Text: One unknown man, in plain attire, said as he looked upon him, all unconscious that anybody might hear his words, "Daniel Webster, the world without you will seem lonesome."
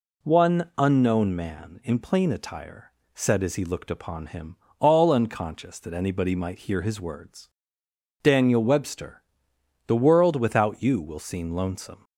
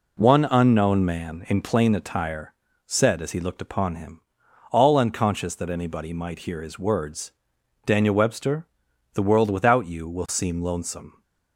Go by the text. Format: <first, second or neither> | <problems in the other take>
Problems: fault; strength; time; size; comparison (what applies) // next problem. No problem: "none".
neither | none